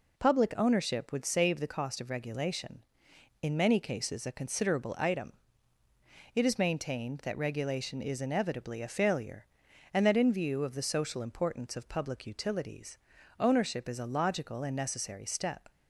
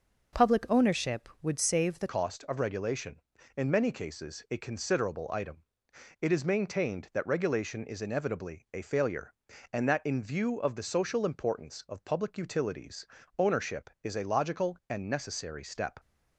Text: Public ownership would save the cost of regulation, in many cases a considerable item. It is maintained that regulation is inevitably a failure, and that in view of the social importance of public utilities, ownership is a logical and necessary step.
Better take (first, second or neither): first